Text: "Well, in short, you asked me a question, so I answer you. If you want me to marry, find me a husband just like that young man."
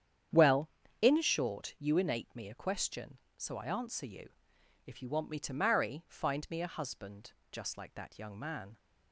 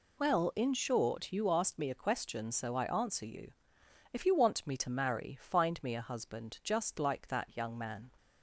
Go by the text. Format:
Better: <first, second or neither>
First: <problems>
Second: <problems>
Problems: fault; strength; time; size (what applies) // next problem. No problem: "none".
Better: second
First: starts louder than the rest; strong; until 1.6 s; 9 dB // says "innate" for "asked"; at 1.9 s // pauses between "husband" and "just"; slight; at 7.3 s; 0.18 s long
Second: none